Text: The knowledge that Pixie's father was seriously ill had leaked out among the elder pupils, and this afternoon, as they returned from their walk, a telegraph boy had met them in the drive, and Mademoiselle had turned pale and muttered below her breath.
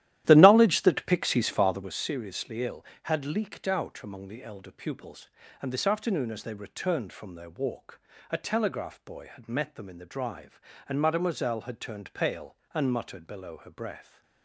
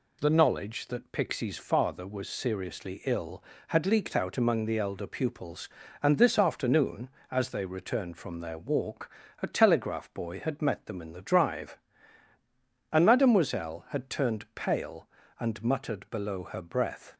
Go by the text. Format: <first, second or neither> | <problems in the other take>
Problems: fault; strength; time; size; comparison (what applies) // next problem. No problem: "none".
second | starts louder than the rest; strong; until 1.9 s; 13.5 dB